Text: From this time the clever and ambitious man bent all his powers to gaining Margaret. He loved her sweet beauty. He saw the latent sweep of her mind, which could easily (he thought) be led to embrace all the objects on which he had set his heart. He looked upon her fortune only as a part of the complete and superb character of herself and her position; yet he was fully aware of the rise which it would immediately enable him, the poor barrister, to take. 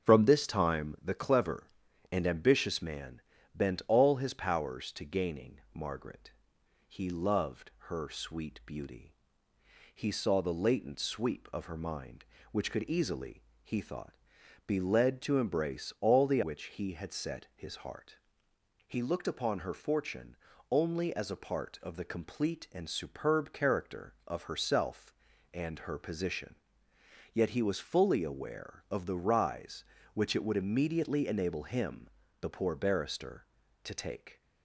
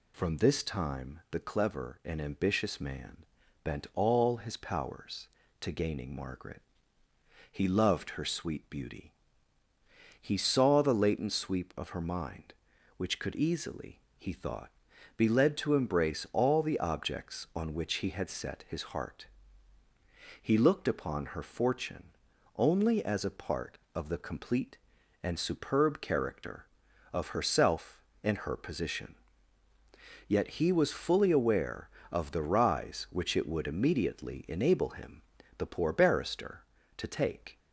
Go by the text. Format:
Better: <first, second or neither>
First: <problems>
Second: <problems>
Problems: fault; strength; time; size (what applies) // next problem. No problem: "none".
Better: second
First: starts louder than the rest; until 1.0 s; 6.5 dB // pauses between "man" and "bent"; slight; at 3.2 s; 0.34 s long // pauses between "loved" and "her"; slight; at 7.7 s; 0.16 s long // skips "objects on"; at 16.4 s // pauses between "fortune" and "only"; slight; at 20.3 s; 0.34 s long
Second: pauses between "man" and "bent"; at 3.2 s; 0.40 s long // pauses between "fortune" and "only"; at 22.1 s; 0.42 s long